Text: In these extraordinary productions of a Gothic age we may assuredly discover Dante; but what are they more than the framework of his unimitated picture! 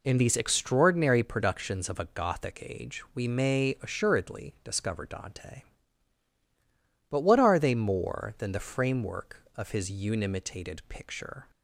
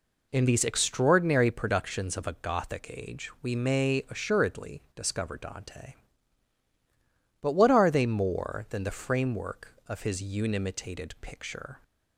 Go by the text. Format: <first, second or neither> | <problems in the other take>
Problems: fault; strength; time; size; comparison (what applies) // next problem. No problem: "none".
neither | none